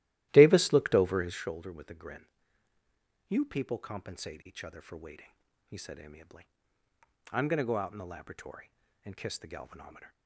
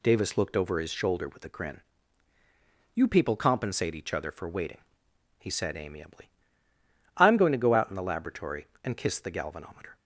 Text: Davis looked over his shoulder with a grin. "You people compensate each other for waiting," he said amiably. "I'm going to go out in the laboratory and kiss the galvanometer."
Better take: second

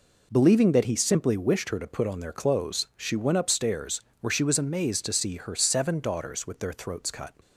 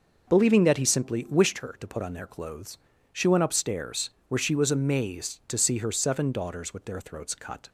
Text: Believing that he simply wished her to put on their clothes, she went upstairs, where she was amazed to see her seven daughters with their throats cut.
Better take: neither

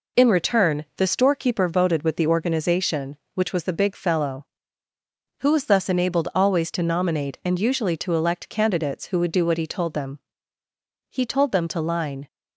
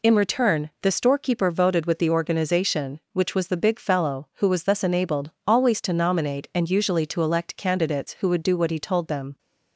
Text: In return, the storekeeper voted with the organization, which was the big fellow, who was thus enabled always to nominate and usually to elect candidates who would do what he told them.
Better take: second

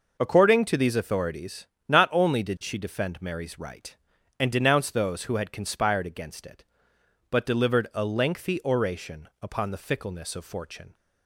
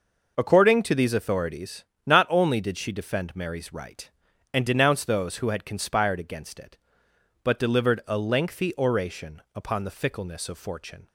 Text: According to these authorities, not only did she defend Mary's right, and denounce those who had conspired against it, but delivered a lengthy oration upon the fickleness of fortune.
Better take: neither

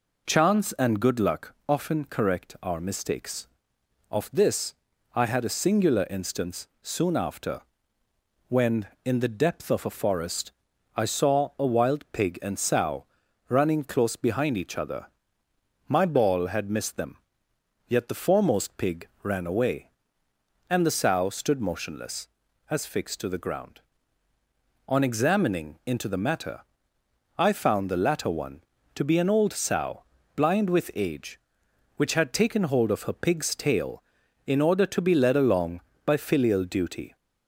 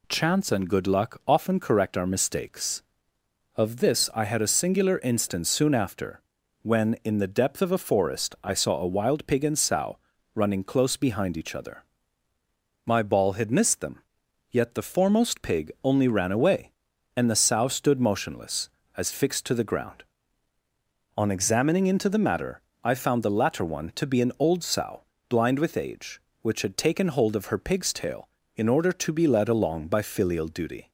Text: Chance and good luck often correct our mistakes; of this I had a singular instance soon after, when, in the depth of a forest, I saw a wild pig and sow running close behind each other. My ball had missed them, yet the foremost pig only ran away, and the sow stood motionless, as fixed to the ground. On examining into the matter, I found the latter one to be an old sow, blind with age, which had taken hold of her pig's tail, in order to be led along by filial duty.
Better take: second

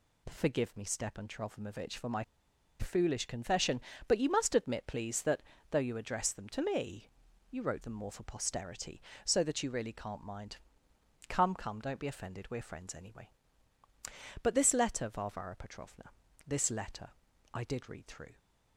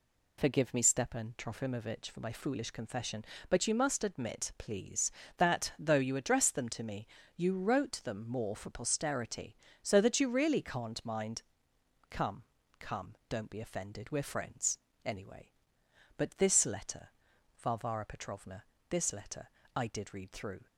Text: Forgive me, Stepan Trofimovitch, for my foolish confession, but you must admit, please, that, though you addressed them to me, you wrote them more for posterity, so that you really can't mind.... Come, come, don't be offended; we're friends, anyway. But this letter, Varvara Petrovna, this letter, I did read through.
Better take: second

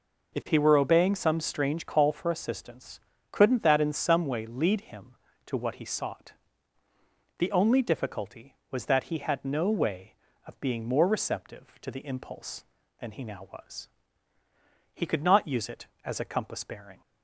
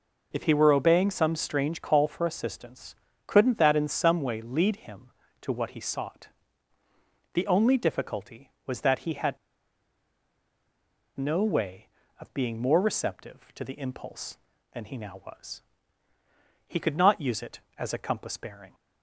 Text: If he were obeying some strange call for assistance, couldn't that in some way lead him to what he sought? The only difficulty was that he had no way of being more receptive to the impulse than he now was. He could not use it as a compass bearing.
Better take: first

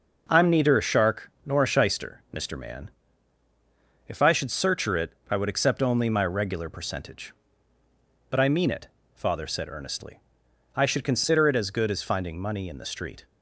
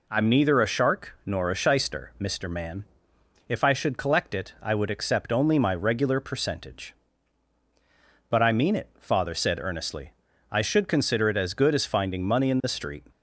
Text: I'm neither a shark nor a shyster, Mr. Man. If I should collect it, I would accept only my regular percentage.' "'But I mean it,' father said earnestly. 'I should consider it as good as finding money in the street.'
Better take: second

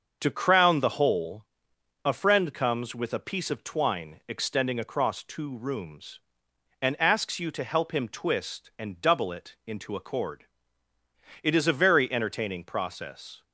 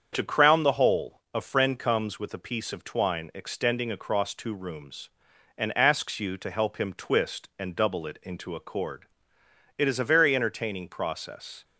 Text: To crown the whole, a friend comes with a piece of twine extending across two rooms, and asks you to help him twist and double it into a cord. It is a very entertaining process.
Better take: neither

